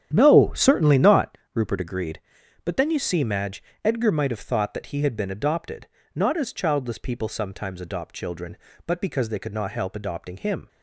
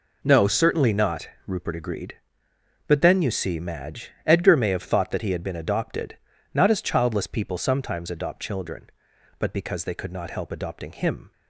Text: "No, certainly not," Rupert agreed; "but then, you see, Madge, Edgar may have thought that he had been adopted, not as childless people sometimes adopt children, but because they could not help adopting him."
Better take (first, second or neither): second